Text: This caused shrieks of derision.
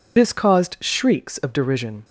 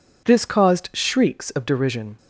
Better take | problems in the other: second | loses the start of "This"; at 0.1 s; 40 ms

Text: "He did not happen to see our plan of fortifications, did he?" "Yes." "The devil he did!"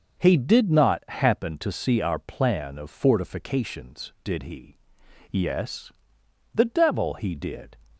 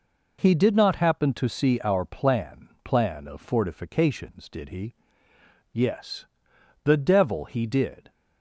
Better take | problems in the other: first | says "plan" twice; at 2.8 s

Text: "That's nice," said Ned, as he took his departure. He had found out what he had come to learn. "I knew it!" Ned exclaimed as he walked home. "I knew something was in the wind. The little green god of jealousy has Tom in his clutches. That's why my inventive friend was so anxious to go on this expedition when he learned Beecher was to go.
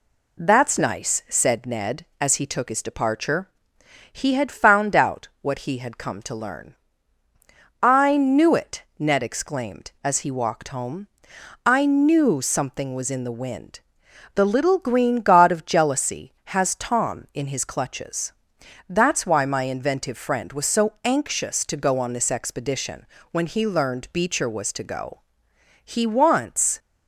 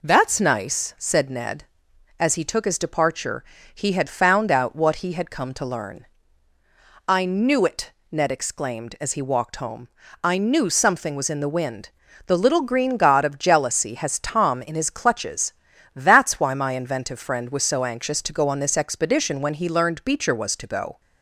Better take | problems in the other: second | pauses between "expedition" and "when"; slight; at 23.0 s; 0.26 s long // goes on to say "He wants"; noticeable; from 25.8 s on; 0.94 s long

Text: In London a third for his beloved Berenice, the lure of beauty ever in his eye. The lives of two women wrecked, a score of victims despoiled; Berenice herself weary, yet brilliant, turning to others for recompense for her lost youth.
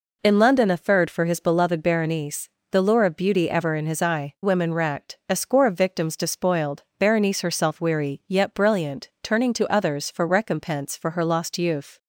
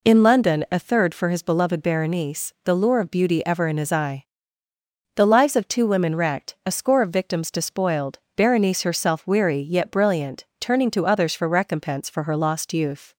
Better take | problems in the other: second | skips "The lives of two"; at 4.3 s

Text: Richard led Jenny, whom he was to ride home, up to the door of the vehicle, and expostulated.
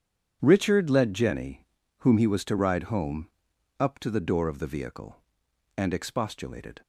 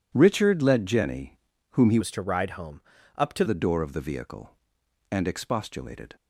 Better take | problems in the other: first | changes voice from "was" to "to"; from 2.0 to 3.4 s; 1.4 s long

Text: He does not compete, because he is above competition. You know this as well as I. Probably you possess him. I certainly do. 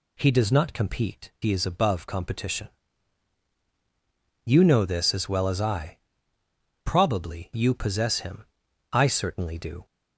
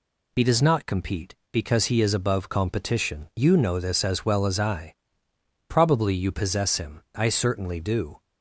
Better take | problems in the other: second | skips "because"; at 1.3 s

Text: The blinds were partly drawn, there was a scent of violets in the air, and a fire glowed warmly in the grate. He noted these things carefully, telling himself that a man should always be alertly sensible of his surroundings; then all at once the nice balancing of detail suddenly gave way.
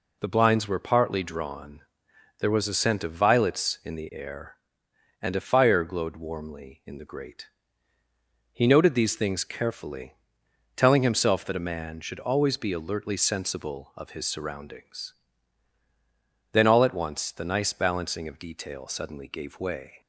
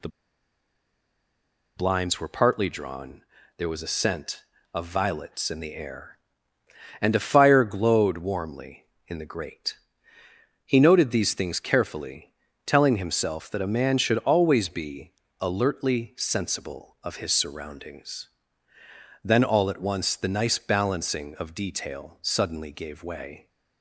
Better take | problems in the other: first | pauses between "The" and "blinds"; strong; at 0.0 s; 1.6 s long // pauses between "be" and "alertly"; slight; at 15.1 s; 0.28 s long

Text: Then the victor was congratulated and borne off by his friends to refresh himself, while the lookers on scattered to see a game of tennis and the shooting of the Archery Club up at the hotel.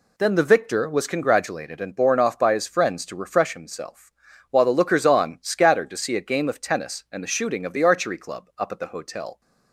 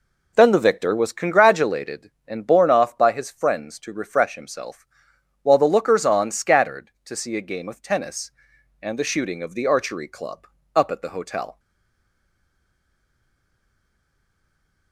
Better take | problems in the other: first | pauses between "Club" and "up"; slight; at 10.4 s; 0.28 s long // stays silent after the last word; strong; from 11.5 s on; 3.4 s long

